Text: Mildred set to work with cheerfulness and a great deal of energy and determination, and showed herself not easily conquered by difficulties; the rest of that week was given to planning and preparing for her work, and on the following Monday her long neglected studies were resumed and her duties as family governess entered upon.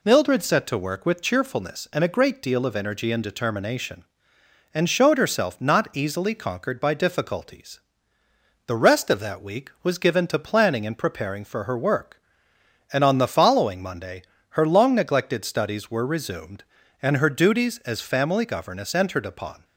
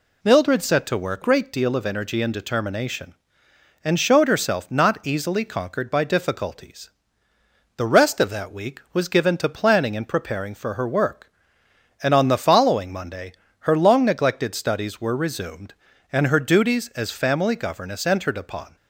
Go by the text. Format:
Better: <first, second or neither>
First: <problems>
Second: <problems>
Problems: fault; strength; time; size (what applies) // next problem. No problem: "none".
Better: first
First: pauses between "Monday" and "her"; slight; at 14.2 s; 0.26 s long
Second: skips "with cheerfulness and a"; at 1.2 s // pauses between "Monday" and "her"; slight; at 13.3 s; 0.26 s long